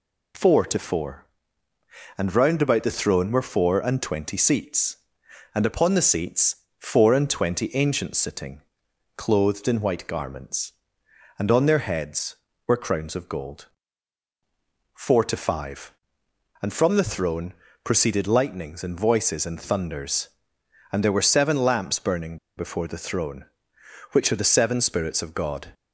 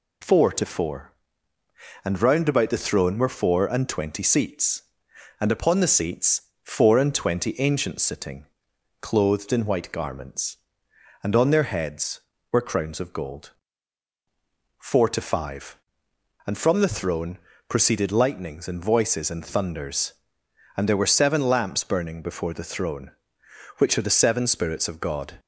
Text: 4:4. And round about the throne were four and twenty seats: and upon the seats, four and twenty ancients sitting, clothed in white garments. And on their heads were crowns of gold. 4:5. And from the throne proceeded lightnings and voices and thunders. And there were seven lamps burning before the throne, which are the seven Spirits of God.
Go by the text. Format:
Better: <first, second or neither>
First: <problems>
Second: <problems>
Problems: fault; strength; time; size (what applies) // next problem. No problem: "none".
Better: second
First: pauses between "throne" and "proceeded"; slight; at 17.5 s; 0.28 s long // pauses between "burning" and "before"; slight; at 22.3 s; 0.21 s long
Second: pauses between "throne" and "proceeded"; slight; at 17.3 s; 0.28 s long